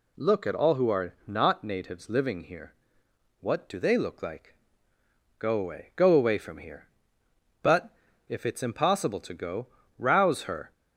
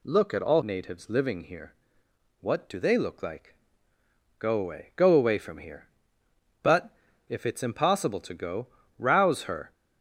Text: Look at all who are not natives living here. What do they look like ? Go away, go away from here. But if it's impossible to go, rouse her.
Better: first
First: pauses between "But" and "if"; at 7.9 s; 0.38 s long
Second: skips "who are not"; at 0.6 s // pauses between "But" and "if"; at 6.9 s; 0.38 s long

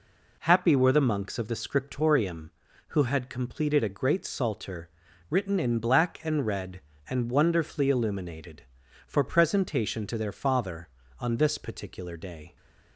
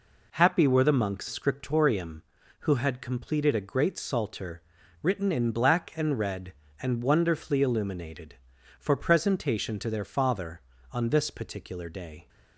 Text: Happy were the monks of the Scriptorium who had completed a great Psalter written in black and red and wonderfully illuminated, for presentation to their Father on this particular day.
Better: first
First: pauses between "Psalter" and "written"; at 4.8 s; 0.40 s long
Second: skips "of the"; at 1.2 s // pauses between "Psalter" and "written"; at 4.6 s; 0.40 s long

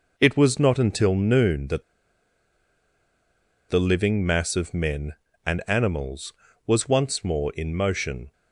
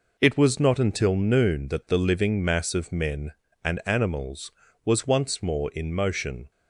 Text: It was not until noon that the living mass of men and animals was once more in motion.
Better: second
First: pauses between "that" and "the"; strong; at 1.8 s; 1.8 s long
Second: none

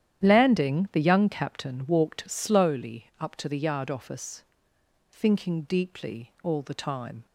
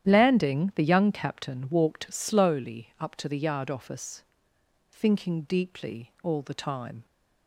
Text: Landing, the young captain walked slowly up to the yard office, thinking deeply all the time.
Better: neither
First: starts louder than the rest; strong; until 1.2 s; 10.5 dB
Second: starts louder than the rest; strong; until 1.1 s; 10.5 dB

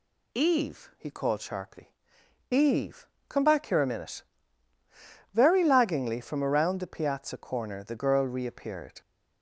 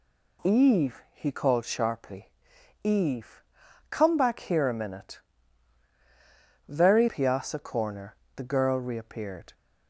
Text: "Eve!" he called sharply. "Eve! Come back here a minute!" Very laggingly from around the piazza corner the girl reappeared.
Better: first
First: none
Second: skips "laggingly from around the"; at 7.0 s // pauses between "corner" and "the"; slight; at 8.1 s; 0.18 s long

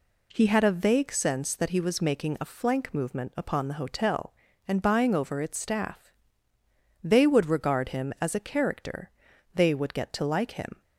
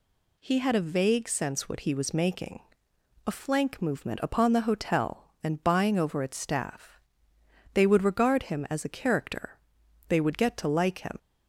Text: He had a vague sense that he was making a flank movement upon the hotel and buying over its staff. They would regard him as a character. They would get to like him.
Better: first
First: none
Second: says "what" for "that"; at 1.6 s // pauses between "making" and "a"; noticeable; at 2.6 s; 0.64 s long

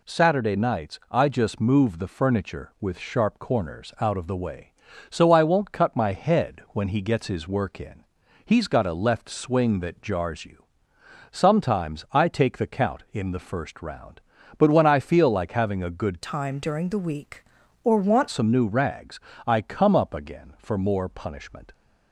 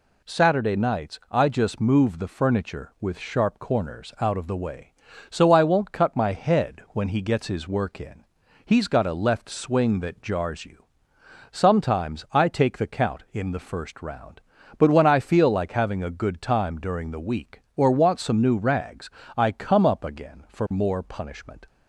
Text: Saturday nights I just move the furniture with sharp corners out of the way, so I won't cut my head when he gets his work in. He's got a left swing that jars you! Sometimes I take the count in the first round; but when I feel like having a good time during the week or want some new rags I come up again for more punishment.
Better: second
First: changes voice from "time" to "want"; from 16.2 to 18.2 s; 2.0 s long // pauses between "rags" and "I"; slight; at 19.2 s; 0.26 s long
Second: pauses between "rags" and "I"; slight; at 19.1 s; 0.26 s long

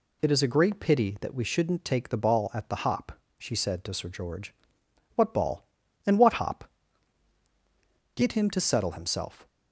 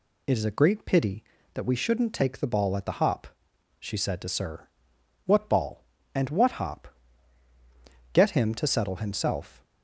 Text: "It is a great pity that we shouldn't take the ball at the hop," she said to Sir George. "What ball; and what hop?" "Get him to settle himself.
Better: first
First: none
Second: skips "George"; at 4.9 s

